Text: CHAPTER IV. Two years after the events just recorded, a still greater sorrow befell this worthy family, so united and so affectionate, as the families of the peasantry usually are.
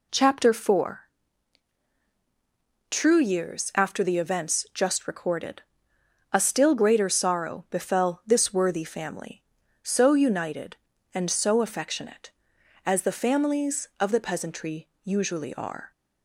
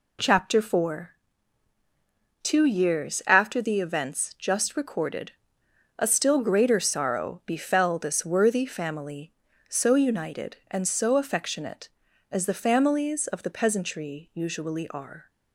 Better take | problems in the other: second | says "True" for "Two"; at 2.8 s // pauses between "peasantry" and "usually"; slight; at 14.8 s; 0.16 s long

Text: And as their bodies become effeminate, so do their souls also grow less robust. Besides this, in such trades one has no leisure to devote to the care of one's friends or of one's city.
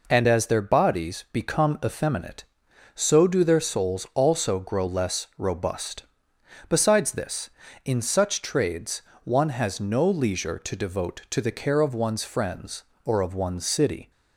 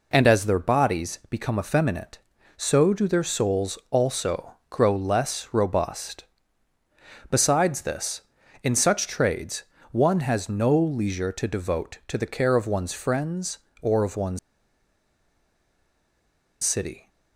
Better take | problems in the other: first | pauses between "also" and "grow"; slight; at 4.5 s; 0.16 s long // pauses between "trades" and "one"; slight; at 9.6 s; 0.28 s long; slight in the first // pauses between "one's" and "city"; strong; at 14.3 s; 2.2 s long

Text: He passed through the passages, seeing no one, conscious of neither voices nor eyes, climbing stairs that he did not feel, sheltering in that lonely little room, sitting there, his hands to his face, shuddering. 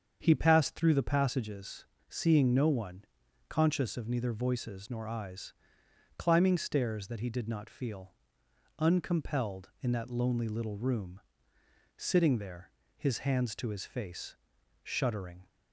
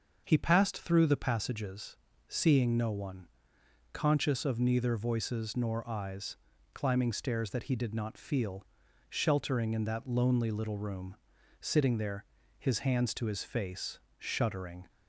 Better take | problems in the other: second | starts louder than the rest; strong; until 1.2 s; 7.5 dB; also in the second // says "uncompelled" for "sheltering"; at 8.7 s

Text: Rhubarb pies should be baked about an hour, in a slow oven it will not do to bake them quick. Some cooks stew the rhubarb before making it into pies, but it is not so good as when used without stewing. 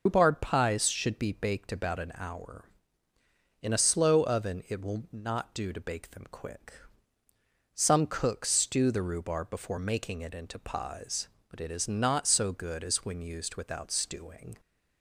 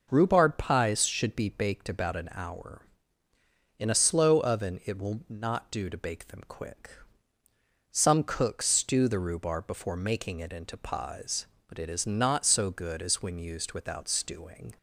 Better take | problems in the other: second | loses the start of "Rhubarb"; at 0.0 s; 120 ms

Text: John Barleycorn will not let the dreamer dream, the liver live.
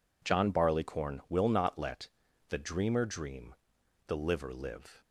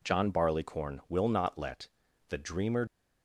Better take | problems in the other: first | pauses between "let" and "the"; at 1.8 s; 0.40 s long; also in the first // stops before "dream the liver live"; at 2.8 s

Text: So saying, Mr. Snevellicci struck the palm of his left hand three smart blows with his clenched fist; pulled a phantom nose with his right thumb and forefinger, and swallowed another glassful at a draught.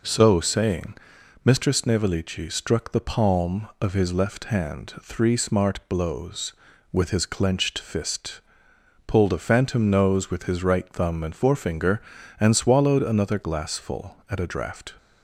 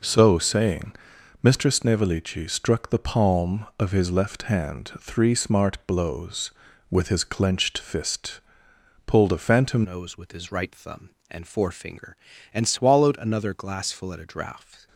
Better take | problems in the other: first | changes voice at "nose"; from 9.8 s on; 5.0 s long

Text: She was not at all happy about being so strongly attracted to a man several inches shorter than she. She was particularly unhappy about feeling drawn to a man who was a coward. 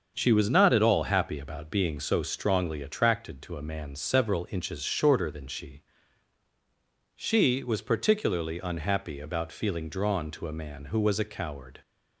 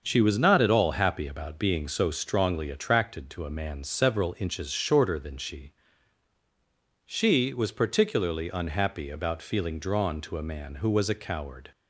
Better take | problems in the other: neither | starts louder than the rest; the same in both

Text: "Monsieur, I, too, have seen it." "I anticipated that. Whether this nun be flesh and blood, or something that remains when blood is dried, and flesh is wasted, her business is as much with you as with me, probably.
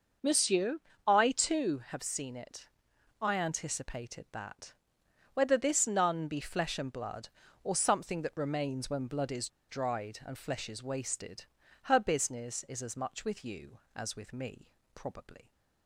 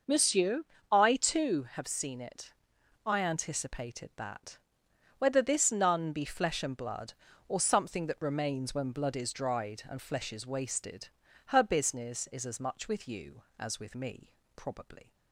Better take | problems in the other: second | starts louder than the rest; noticeable; until 1.5 s; 6 dB // pauses between "is" and "dried"; slight; at 9.4 s; 0.21 s long

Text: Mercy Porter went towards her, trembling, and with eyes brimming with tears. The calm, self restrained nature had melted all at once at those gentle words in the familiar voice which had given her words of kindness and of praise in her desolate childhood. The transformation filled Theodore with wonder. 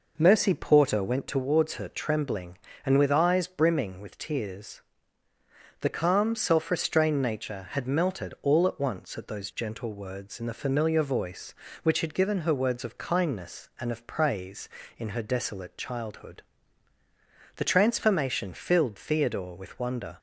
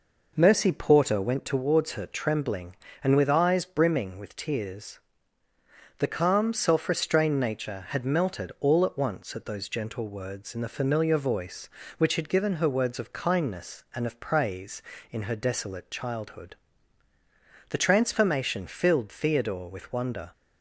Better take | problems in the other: neither | none

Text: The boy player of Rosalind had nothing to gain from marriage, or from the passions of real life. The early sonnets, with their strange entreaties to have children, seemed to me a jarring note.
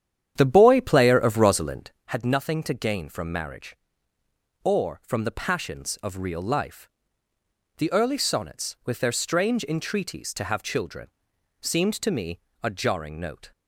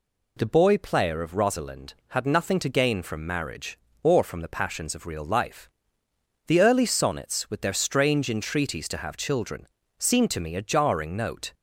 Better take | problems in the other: second | starts louder than the rest; strong; until 2.1 s; 9.5 dB // pauses between "me" and "a"; slight; at 12.3 s; 0.22 s long

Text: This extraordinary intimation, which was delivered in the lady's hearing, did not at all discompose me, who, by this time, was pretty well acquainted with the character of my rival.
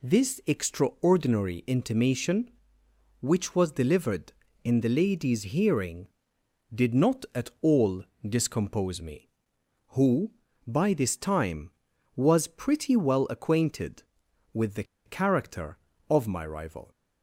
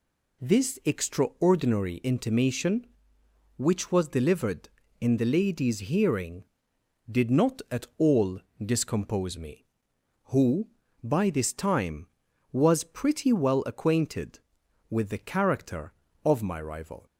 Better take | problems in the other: second | pauses between "all" and "discompose"; slight; at 8.0 s; 0.20 s long; slight in the second // pauses between "the" and "character"; slight; at 14.8 s; 0.22 s long

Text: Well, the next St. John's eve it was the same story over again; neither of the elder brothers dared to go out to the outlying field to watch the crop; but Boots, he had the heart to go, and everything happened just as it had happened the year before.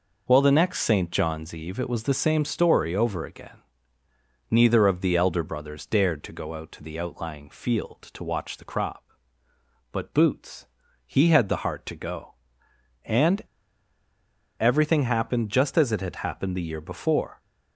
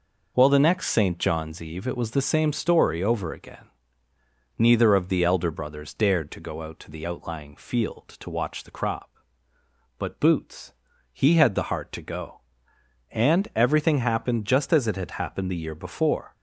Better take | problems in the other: second | pauses between "and" and "everything"; at 13.4 s; 1.1 s long

